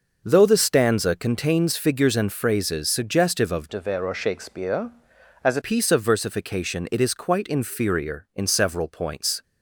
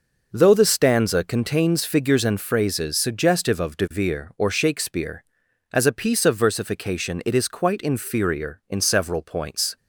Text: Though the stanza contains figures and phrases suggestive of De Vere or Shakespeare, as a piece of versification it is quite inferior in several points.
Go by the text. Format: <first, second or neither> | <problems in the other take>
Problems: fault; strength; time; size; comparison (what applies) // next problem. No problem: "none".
second | changes voice from "De" to "a"; from 3.6 to 5.6 s; 2.0 s long